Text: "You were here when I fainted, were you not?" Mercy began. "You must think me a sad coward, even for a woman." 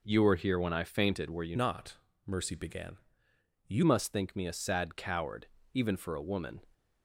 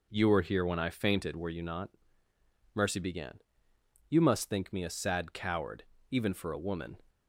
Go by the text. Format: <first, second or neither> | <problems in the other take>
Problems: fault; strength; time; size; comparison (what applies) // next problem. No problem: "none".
second | changes voice from "not" to "You"; from 1.5 to 3.8 s; 2.3 s long